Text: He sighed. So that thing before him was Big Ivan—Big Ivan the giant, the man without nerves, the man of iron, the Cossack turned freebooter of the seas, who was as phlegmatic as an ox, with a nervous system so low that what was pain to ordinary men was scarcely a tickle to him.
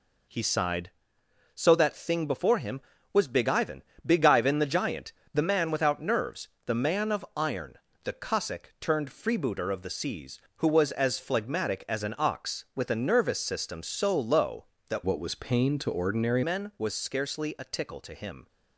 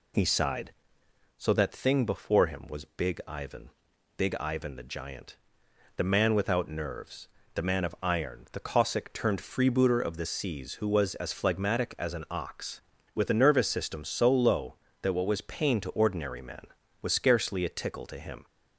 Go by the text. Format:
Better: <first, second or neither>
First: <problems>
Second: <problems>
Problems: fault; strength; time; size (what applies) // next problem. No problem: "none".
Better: second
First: changes voice from "what" to "ordinary"; from 15.0 to 16.4 s; 1.4 s long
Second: none